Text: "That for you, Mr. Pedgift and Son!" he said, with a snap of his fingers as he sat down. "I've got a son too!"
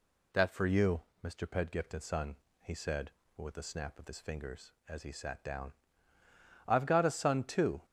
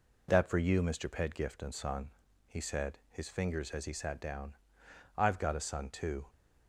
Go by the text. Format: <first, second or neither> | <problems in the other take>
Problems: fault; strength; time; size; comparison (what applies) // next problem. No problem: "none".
first | skips "with a snap of"; at 3.0 s